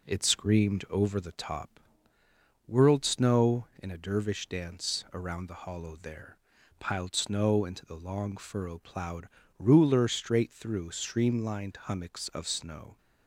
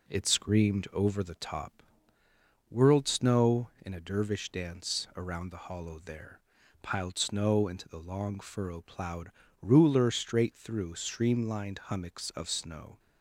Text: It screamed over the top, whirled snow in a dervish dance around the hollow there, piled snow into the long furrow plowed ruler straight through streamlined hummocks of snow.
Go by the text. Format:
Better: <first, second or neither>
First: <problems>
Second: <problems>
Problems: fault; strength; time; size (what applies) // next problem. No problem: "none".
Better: neither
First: pauses between "plowed" and "ruler"; slight; at 9.2 s; 0.30 s long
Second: pauses between "plowed" and "ruler"; slight; at 9.2 s; 0.30 s long